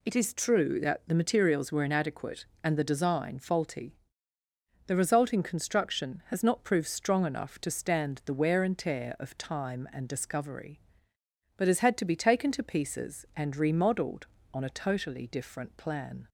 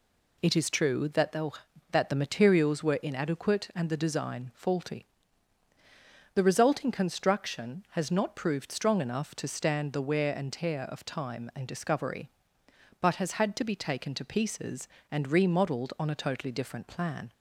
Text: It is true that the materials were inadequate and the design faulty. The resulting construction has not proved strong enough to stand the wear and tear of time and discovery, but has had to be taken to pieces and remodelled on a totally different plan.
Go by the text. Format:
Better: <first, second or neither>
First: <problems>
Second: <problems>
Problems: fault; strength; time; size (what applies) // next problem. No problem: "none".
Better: first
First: none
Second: says "that" twice; at 1.9 s